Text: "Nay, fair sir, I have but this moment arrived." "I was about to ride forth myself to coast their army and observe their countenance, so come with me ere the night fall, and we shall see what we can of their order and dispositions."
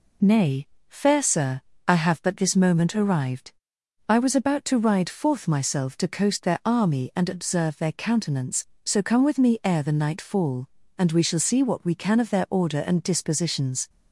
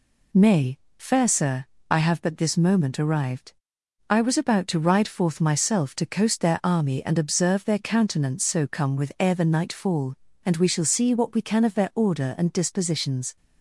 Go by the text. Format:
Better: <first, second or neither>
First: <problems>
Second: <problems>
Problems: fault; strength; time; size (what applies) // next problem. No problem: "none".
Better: first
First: none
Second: skips "me"; at 9.1 s